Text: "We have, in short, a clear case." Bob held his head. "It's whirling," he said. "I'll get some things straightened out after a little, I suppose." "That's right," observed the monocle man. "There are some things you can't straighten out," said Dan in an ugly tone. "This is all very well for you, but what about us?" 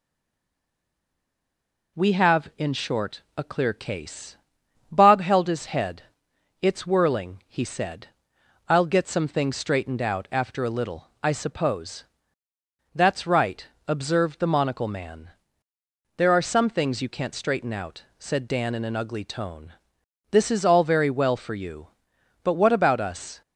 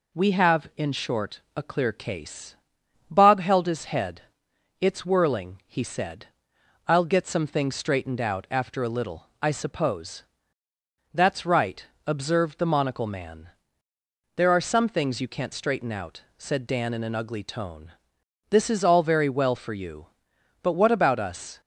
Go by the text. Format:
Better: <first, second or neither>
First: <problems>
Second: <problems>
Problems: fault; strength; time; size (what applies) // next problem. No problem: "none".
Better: second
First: stays silent before the first word; noticeable; until 1.9 s; 1.9 s long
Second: none